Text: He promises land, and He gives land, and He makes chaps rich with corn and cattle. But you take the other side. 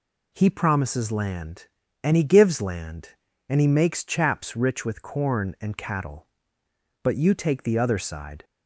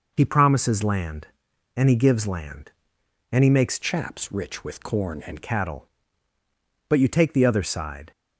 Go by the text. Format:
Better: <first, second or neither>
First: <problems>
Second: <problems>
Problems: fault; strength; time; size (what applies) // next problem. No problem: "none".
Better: first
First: none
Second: changes voice from "chaps" to "and"; from 3.8 to 5.4 s; 1.6 s long